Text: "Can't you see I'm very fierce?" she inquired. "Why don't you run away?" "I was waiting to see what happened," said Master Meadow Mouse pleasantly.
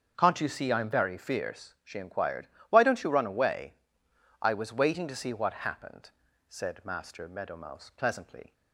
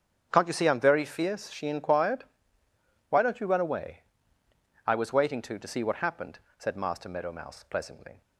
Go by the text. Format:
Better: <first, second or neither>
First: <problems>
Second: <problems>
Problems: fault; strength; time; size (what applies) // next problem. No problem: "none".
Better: first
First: starts louder than the rest; until 1.1 s; 7 dB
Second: starts louder than the rest; strong; until 1.3 s; 8 dB // says "to" twice; at 5.5 s